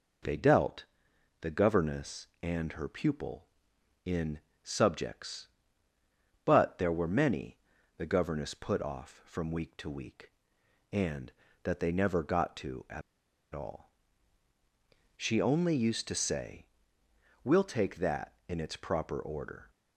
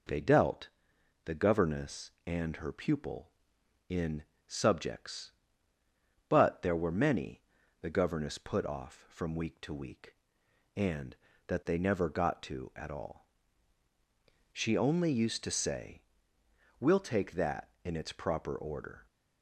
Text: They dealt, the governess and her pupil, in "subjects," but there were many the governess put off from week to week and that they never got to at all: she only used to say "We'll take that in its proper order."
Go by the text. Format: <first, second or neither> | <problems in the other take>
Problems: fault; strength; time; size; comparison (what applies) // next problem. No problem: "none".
second | pauses between "in" and "subjects"; slight; at 4.3 s; 0.22 s long; slight in the second // pauses between "many" and "the"; at 7.5 s; 0.40 s long; also in the second // pauses between "at" and "all"; noticeable; at 13.0 s; 0.52 s long // pauses between "say" and "We'll"; noticeable; at 16.6 s; 0.78 s long; noticeable in the second